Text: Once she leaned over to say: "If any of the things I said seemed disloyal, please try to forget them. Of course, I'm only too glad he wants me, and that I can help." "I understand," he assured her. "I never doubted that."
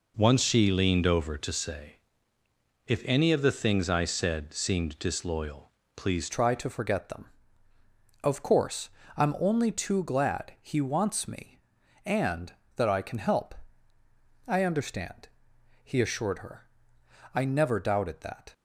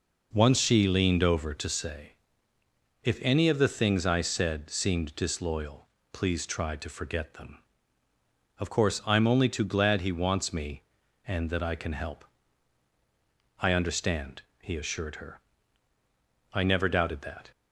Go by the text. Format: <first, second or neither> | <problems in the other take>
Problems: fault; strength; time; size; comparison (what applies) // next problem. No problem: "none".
second | changes voice at "try"; from 6.3 s on; 12.2 s long